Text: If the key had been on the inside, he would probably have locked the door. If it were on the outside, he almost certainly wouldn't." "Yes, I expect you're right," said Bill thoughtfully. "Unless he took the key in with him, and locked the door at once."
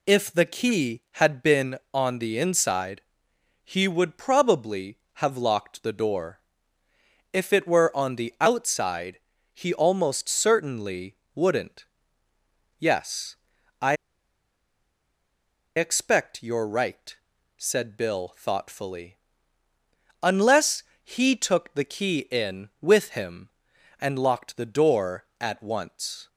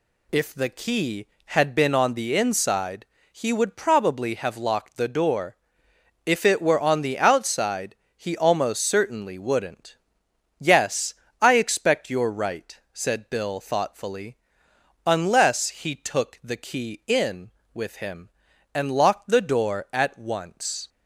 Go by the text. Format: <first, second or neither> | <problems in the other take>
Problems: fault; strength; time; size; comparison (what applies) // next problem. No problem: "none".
second | pauses between "certainly" and "wouldn't"; slight; at 11.1 s; 0.22 s long // pauses between "I" and "expect"; strong; at 13.9 s; 1.8 s long // pauses between "Unless" and "he"; slight; at 20.8 s; 0.18 s long